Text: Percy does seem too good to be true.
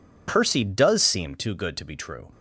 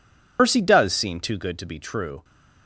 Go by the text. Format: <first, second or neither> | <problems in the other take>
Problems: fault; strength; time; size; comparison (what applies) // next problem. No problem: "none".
first | loses the start of "Percy"; at 0.3 s; 85 ms